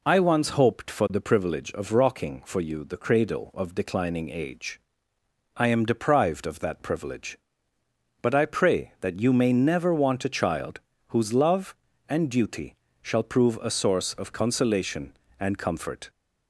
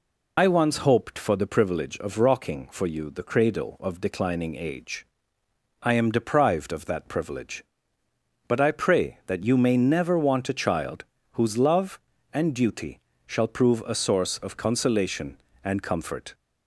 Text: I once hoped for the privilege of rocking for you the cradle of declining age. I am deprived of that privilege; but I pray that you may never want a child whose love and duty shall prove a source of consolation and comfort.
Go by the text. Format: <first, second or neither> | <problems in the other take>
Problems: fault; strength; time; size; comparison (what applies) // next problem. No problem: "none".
first | loses the start of "I"; at 0.3 s; 50 ms // pauses between "child" and "whose"; slight; at 11.0 s; 0.28 s long; slight in the first // pauses between "duty" and "shall"; slight; at 13.0 s; 0.26 s long; slight in the first